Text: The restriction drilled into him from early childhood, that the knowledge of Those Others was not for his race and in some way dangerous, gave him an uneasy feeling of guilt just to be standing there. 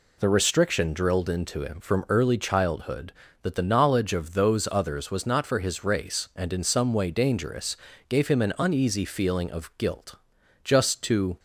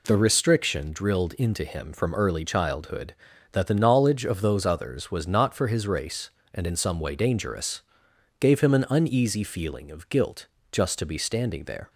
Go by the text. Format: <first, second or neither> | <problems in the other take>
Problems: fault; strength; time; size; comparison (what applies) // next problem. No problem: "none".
second | pauses between "guilt" and "just"; noticeable; at 10.1 s; 0.48 s long; slight in the second // stops before "be standing there"; at 11.3 s